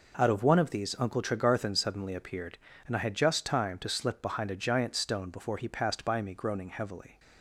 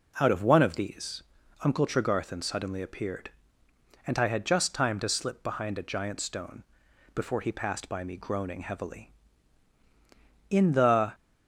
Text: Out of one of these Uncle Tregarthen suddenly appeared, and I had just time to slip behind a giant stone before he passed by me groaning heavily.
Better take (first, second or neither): first